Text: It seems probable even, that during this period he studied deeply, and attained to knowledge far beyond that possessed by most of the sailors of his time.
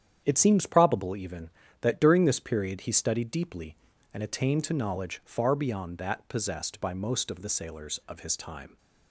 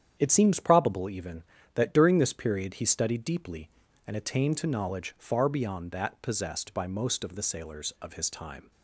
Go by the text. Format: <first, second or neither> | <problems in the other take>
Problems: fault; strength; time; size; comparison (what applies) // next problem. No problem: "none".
neither | starts louder than the rest; strong; the same in both